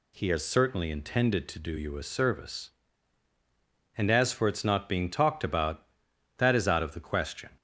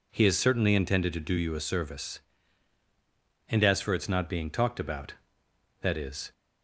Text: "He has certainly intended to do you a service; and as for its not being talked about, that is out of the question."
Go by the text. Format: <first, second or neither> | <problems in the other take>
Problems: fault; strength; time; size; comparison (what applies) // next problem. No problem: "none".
first | stops before "out of the question"; at 6.3 s